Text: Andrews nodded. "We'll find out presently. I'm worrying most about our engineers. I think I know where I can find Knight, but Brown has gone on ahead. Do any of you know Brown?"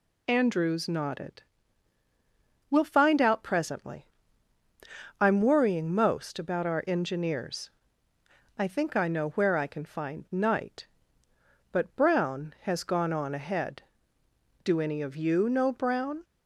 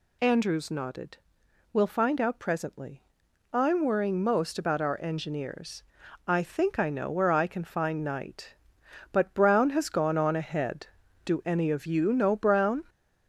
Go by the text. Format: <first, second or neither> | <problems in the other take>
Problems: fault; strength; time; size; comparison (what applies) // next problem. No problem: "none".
first | gets louder; throughout; 4 dB